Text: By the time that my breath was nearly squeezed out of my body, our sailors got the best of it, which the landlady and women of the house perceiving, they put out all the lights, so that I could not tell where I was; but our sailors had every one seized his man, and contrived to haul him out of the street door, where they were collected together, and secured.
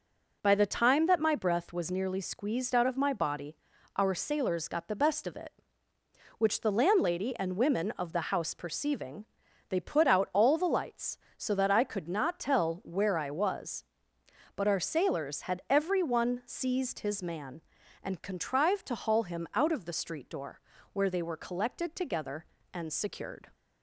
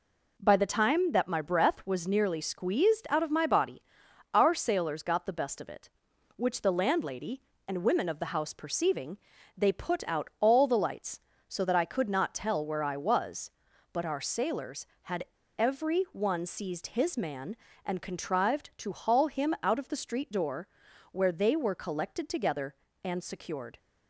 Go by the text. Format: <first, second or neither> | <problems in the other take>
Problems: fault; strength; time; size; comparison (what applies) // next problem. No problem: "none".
first | pauses between "had" and "every"; slight; at 15.2 s; 0.34 s long